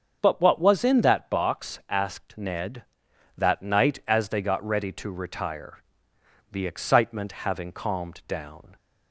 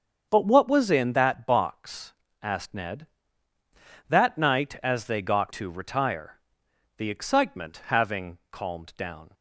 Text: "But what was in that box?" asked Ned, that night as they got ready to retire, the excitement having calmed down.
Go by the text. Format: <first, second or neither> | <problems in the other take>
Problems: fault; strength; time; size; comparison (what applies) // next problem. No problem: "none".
first | starts louder than the rest; strong; until 1.3 s; 7 dB; also in the first // skips "ready"; at 5.5 s